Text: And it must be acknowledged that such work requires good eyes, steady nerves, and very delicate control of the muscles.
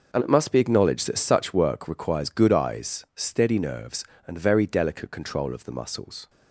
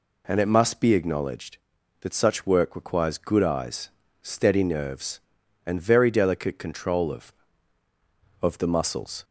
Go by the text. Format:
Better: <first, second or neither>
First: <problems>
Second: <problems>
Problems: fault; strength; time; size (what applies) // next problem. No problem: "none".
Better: first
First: none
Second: says "of" twice; at 8.4 s